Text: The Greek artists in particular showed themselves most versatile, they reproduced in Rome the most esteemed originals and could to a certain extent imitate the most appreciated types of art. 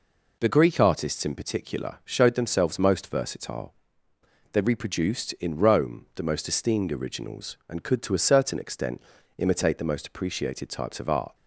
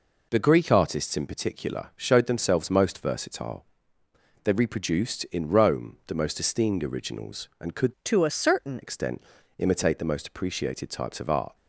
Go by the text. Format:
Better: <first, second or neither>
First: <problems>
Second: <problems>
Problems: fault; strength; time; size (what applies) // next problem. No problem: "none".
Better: first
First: pauses between "extent" and "imitate"; slight; at 9.0 s; 0.36 s long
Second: changes voice from "to" to "certain"; from 8.0 to 8.7 s; 0.7 s long // pauses between "extent" and "imitate"; slight; at 9.2 s; 0.36 s long